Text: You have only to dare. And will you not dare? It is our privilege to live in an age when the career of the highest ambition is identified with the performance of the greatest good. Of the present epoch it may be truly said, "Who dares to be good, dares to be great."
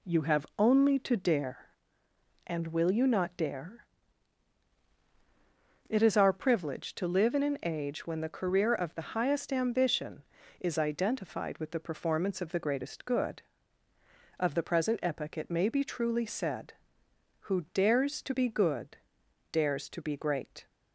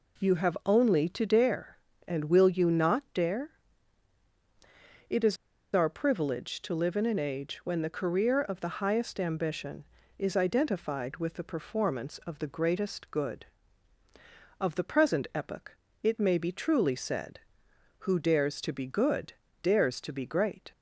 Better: first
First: none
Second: pauses between "is" and "our"; at 5.3 s; 0.37 s long // pauses between "epoch" and "it"; slight; at 15.7 s; 0.26 s long

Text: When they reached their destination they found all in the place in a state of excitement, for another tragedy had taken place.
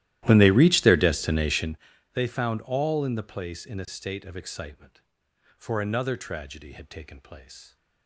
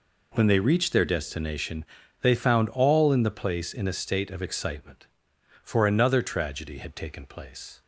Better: second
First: starts louder than the rest; strong; until 1.8 s; 14.5 dB // pauses between "destination" and "they"; at 1.7 s; 0.38 s long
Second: pauses between "destination" and "they"; at 1.8 s; 0.38 s long

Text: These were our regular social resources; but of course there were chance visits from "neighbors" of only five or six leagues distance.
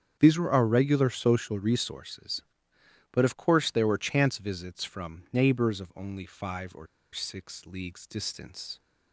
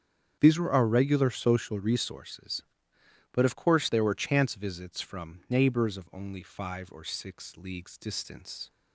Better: second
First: starts louder than the rest; strong; until 1.2 s; 8 dB // pauses between "or" and "six"; slight; at 6.8 s; 0.26 s long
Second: starts louder than the rest; strong; until 1.4 s; 8 dB

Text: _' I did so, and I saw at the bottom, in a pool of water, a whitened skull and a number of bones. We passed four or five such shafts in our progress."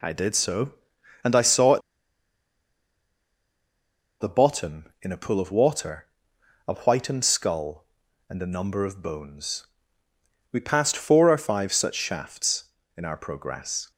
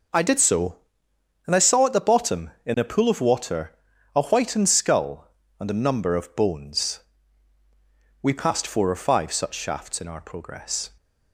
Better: second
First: pauses between "at" and "the"; strong; at 1.8 s; 2.4 s long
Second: none

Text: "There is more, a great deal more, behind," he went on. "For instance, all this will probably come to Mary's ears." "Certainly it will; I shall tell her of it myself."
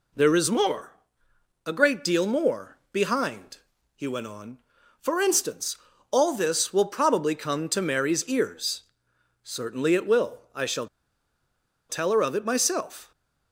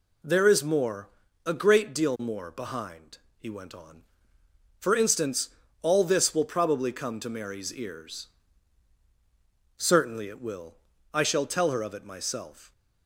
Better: second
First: pauses between "shall" and "tell"; at 10.8 s; 1.0 s long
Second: none

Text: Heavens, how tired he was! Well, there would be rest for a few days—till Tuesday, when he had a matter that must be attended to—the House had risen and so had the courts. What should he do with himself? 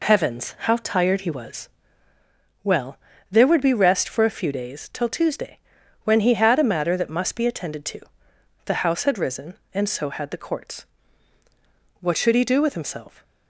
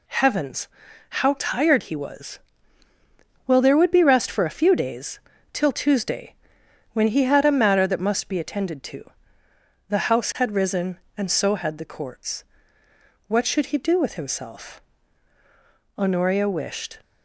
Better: first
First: none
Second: goes on to say "Honoria wished"; noticeable; from 15.9 s on; 1.0 s long

